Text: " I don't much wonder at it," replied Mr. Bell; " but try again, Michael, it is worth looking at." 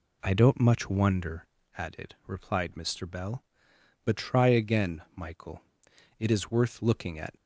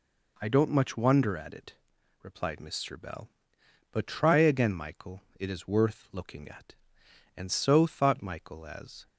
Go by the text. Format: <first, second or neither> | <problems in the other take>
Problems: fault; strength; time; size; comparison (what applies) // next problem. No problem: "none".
first | goes on to say "And so thought Michael as"; strong; from 7.3 s on; 1.7 s long